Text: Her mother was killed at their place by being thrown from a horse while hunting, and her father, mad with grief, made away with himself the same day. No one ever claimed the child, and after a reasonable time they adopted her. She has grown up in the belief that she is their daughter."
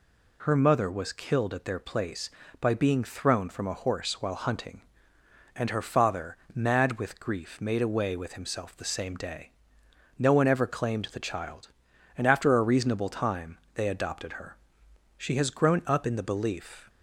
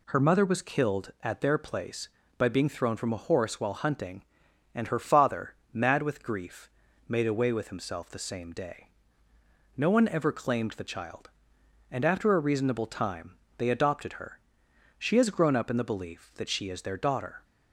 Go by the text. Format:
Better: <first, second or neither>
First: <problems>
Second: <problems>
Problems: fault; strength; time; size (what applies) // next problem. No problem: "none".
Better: second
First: pauses between "time" and "they"; slight; at 13.5 s; 0.16 s long // stops before "that she is their daughter"; at 16.8 s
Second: pauses between "time" and "they"; slight; at 13.3 s; 0.20 s long